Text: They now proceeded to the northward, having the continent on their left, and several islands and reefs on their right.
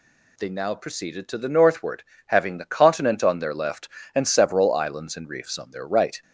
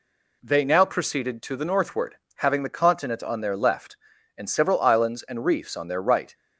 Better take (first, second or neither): neither